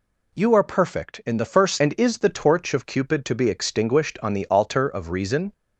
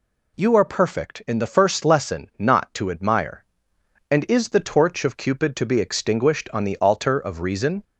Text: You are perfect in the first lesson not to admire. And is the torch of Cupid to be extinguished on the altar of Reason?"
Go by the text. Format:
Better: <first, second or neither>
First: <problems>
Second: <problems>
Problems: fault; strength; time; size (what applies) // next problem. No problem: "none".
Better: second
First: skips "lesson not to admire"; at 1.7 s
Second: none